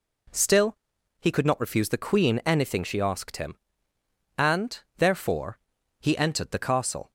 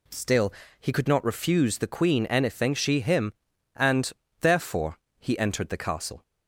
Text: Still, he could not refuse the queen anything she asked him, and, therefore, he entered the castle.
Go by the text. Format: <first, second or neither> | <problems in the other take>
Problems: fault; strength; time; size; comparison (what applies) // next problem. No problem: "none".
first | skips "asked"; at 3.0 s